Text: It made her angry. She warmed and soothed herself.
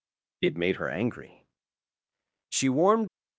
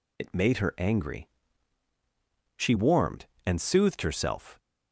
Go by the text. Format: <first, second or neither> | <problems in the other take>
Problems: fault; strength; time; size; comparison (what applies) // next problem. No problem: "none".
second | stops before "and soothed herself"; at 3.0 s